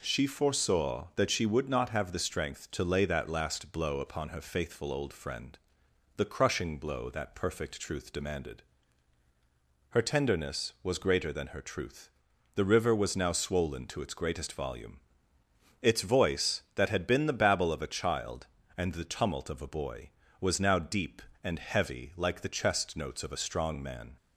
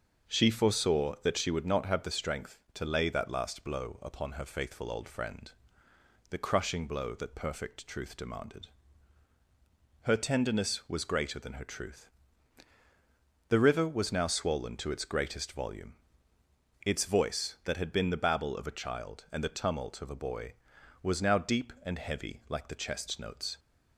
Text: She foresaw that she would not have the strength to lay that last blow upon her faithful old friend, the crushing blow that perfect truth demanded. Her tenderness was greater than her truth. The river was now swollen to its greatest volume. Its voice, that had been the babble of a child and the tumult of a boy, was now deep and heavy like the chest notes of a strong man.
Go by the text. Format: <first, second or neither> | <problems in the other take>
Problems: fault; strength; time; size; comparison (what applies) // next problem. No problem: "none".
first | starts louder than the rest; until 1.3 s; 6.5 dB // stops before "of a strong man"; at 23.5 s